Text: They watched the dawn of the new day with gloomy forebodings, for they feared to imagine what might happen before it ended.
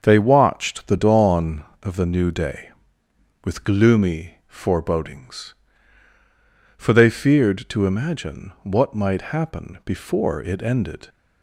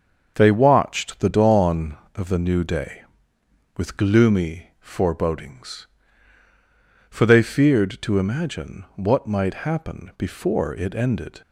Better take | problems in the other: neither | starts louder than the rest; the same in both

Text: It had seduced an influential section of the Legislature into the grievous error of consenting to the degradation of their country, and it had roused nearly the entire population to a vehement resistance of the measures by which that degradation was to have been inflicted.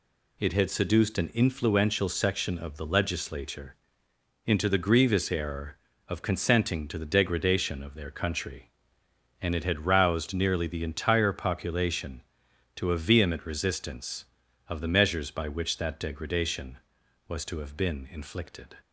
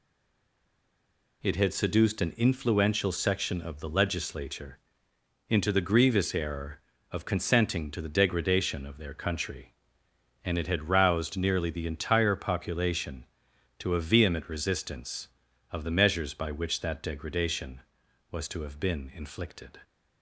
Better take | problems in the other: first | stays silent before the first word; noticeable; until 1.4 s; 1.4 s long // pauses between "Legislature" and "into"; noticeable; at 4.7 s; 0.70 s long; noticeable in the first

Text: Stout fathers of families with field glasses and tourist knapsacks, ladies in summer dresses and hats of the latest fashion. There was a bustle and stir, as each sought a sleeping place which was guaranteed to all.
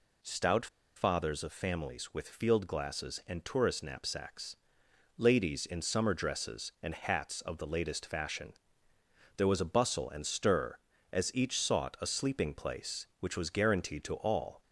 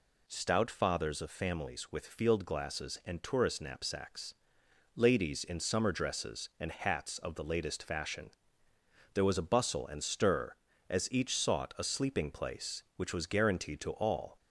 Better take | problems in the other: second | pauses between "Stout" and "fathers"; slight; at 0.6 s; 0.29 s long

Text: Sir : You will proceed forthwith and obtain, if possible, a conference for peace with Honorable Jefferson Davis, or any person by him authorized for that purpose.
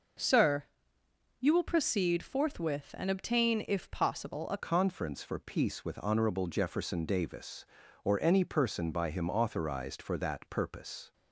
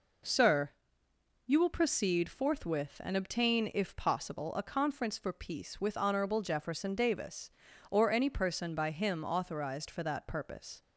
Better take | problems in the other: second | changes voice at "conference"; from 4.5 s on; 6.6 s long

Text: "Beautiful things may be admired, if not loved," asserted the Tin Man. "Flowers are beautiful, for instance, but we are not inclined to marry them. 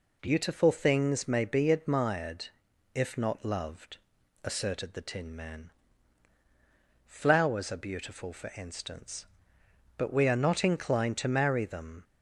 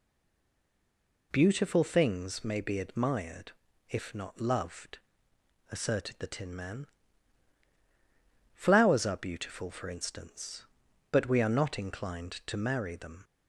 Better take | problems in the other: first | stays silent before the first word; noticeable; until 1.3 s; 1.3 s long

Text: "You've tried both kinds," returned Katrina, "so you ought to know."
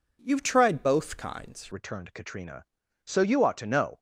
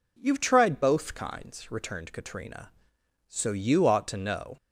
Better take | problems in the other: second | changes voice at "returned"; from 1.7 s on; 2.2 s long

